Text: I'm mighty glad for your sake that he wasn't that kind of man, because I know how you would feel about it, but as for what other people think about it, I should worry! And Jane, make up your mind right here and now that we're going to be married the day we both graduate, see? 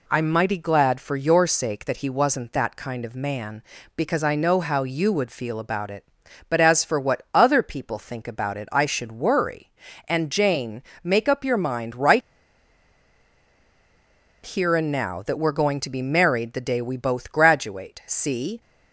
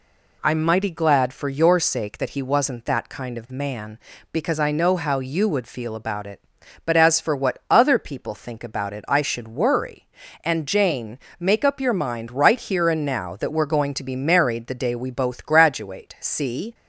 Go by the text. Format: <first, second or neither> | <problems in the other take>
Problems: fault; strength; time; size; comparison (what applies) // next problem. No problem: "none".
second | pauses between "right" and "here"; strong; at 12.2 s; 2.2 s long